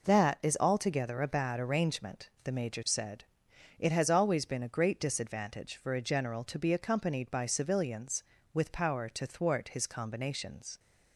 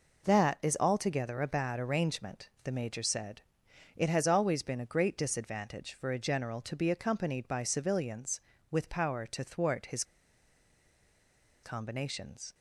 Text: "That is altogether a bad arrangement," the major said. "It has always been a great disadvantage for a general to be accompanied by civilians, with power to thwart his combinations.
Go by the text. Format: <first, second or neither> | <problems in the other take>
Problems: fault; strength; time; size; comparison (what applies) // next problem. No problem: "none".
first | pauses between "his" and "combinations"; strong; at 10.0 s; 1.6 s long